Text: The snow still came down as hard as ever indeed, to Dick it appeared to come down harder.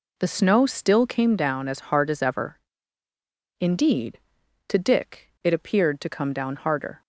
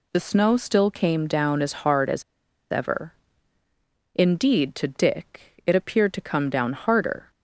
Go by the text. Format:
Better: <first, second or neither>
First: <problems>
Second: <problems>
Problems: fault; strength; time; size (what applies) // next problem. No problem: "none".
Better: first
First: pauses between "ever" and "indeed"; at 2.5 s; 1.0 s long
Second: pauses between "as" and "ever"; noticeable; at 2.2 s; 0.49 s long // pauses between "ever" and "indeed"; at 3.1 s; 1.0 s long